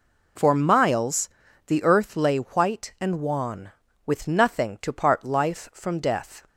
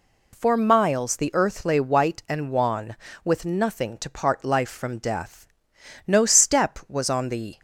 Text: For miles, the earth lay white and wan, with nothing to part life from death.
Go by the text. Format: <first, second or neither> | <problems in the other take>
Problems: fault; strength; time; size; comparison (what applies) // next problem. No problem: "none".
first | goes on to say "No step was on the"; from 6.0 s on; 1.5 s long